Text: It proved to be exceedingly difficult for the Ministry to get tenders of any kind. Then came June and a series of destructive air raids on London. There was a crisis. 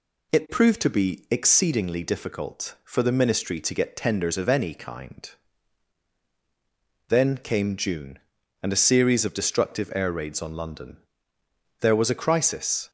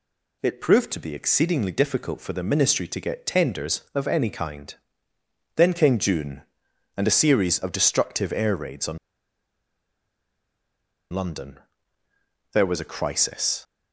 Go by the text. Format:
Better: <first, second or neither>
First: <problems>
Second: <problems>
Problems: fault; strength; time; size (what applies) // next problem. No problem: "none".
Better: first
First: none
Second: pauses between "on" and "London"; strong; at 8.9 s; 2.1 s long